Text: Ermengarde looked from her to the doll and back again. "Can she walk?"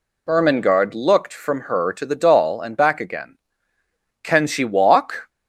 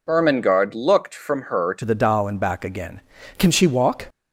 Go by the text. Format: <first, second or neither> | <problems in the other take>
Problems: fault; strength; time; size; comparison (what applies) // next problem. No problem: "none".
first | changes voice at "the"; from 1.8 s on; 2.2 s long